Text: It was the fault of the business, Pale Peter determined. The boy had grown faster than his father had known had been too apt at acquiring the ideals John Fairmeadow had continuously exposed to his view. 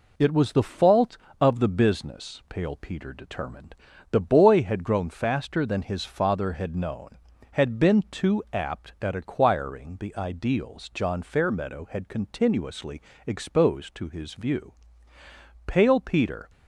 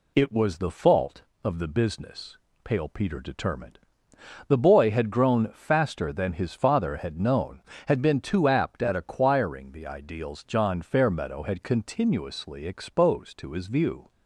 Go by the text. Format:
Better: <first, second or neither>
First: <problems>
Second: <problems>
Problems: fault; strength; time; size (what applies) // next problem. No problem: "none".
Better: second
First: pauses between "continuously" and "exposed"; slight; at 12.9 s; 0.26 s long // goes on to say "Pale Peter"; noticeable; from 15.6 s on; 0.84 s long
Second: none